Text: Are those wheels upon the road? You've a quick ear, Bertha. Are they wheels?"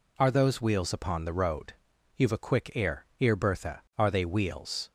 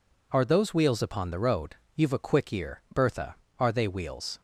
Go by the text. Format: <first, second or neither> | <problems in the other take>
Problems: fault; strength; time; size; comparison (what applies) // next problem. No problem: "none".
second | says "ear" twice; at 3.1 s